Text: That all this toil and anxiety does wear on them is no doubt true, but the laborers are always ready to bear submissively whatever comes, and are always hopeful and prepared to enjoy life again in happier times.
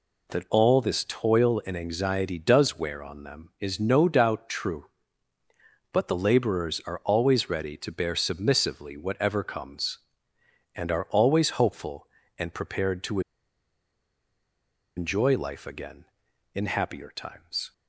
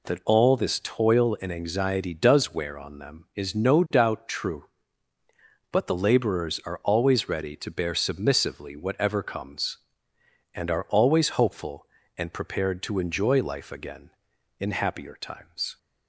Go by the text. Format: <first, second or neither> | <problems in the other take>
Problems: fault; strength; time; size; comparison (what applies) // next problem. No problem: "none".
second | pauses between "to" and "enjoy"; strong; at 13.2 s; 1.7 s long